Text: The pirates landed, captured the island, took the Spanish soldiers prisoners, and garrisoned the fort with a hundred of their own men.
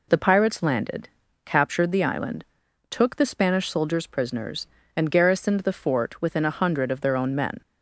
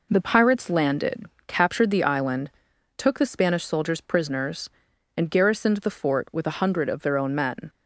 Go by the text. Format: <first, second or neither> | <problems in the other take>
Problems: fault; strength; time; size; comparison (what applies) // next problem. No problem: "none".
second | says "within" for "with"; at 6.1 s